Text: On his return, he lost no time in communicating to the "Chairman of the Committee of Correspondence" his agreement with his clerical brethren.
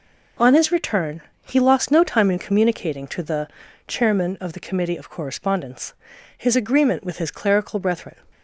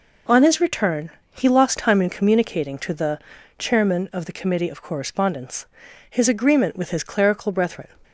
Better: first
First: pauses between "the" and "Chairman"; at 3.4 s; 0.40 s long // pauses between "Correspondence" and "his"; at 5.9 s; 0.42 s long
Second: skips "no"; at 1.7 s // pauses between "the" and "Chairman"; at 3.1 s; 0.40 s long // pauses between "Correspondence" and "his"; at 5.6 s; 0.42 s long

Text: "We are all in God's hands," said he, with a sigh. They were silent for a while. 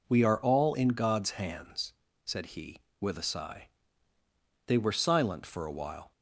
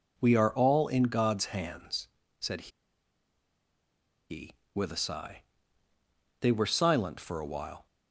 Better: first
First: none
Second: pauses between "said" and "he"; strong; at 2.7 s; 1.6 s long

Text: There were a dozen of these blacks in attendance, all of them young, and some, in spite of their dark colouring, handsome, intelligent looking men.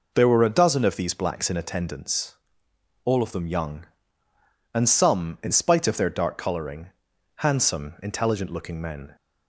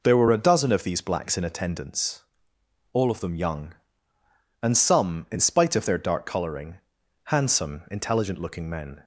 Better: neither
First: none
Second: none

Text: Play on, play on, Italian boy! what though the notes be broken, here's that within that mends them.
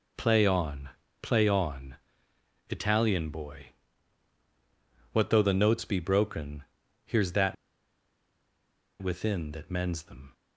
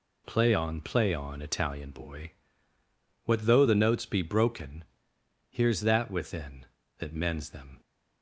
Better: second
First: pauses between "that" and "within"; strong; at 7.5 s; 1.4 s long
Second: none

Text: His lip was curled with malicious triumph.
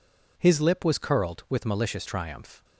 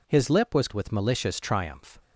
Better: first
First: none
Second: skips "curled"; at 0.7 s

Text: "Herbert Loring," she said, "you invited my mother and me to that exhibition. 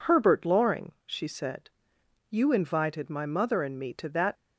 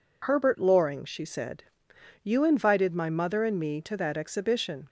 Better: second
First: stops before "exhibition"; at 4.3 s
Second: none

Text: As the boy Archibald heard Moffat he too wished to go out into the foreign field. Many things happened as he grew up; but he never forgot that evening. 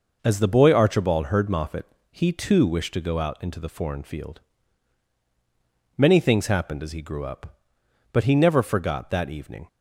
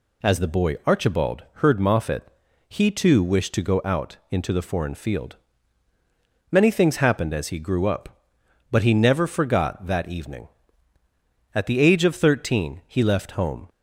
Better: first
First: pauses between "Moffat" and "he"; slight; at 1.8 s; 0.26 s long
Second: pauses between "Moffat" and "he"; at 2.2 s; 0.44 s long // goes on to say "At the age of thirteen he left home"; strong; from 11.5 s on; 2.1 s long

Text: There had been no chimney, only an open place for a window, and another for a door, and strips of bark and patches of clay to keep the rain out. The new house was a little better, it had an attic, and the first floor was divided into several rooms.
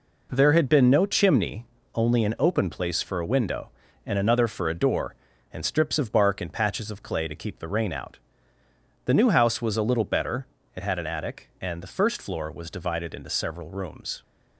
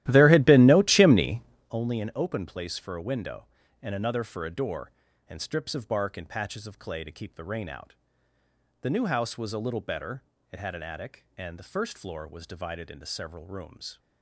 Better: first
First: none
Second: starts louder than the rest; strong; until 1.8 s; 14.5 dB

